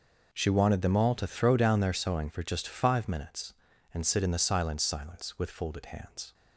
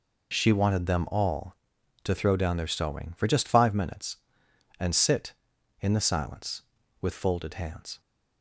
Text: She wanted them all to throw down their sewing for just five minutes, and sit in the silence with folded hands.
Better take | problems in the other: second | says "silence" twice; at 4.8 s

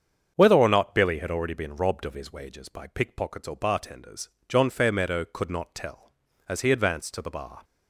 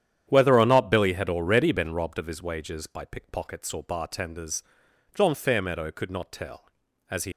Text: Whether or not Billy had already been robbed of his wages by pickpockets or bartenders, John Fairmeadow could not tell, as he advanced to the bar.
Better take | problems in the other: first | starts louder than the rest; strong; until 1.2 s; 9.5 dB; strong in the first // stops before "advanced to the bar"; at 7.3 s

